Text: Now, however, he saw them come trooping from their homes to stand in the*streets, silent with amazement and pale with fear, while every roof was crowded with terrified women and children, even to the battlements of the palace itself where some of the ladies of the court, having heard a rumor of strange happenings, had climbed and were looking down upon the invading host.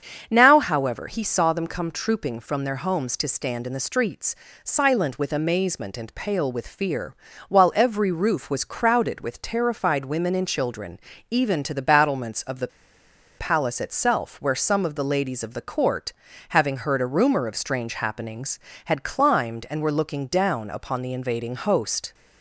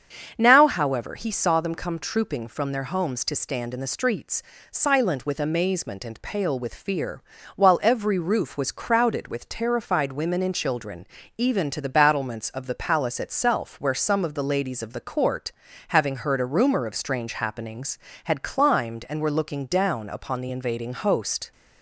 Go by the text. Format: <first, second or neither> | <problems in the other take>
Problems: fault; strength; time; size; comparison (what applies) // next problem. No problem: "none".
second | starts louder than the rest; until 1.3 s; 7 dB; also in the second // pauses between "the" and "palace"; noticeable; at 12.6 s; 0.71 s long